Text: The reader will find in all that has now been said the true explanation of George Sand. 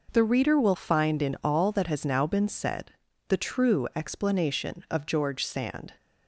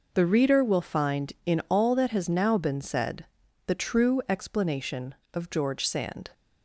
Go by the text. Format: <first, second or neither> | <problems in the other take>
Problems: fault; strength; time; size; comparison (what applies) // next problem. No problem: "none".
neither | pauses between "said" and "the"; the same in both